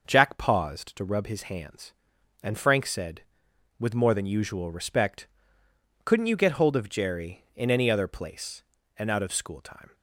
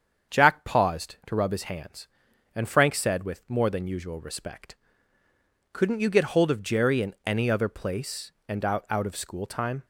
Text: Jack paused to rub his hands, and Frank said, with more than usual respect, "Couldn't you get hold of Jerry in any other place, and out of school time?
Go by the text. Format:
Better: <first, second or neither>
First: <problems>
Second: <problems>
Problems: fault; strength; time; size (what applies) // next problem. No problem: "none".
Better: first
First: none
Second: starts louder than the rest; strong; until 1.4 s; 7.5 dB // says "out" twice; at 8.9 s